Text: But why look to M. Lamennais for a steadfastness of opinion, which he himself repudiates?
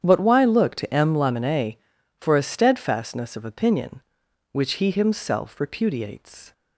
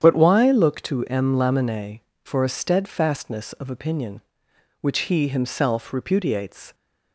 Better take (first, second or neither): neither